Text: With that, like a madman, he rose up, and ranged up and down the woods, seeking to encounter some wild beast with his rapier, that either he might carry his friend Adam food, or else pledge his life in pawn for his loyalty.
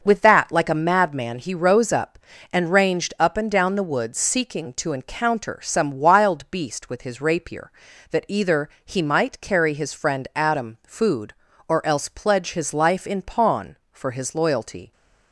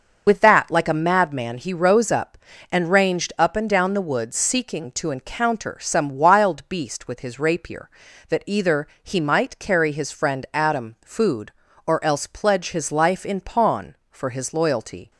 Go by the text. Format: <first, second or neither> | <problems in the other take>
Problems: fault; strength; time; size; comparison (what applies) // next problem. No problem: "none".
first | loses the start of "With"; at 0.2 s; 70 ms // starts louder than the rest; until 1.2 s; 6.5 dB; also in the first // pauses between "either" and "he"; slight; at 8.8 s; 0.16 s long; slight in the first